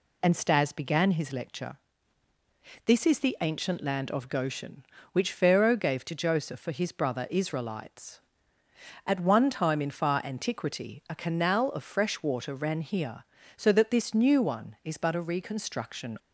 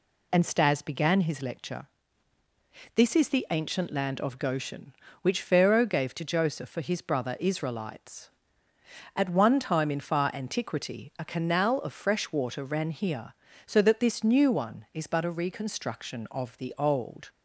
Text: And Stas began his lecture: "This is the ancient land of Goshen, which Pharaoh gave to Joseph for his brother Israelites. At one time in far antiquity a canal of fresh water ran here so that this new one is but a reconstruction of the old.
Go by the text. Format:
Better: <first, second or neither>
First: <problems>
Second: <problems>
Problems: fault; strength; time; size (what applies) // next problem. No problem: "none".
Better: second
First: stops before "of the old"; at 16.1 s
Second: none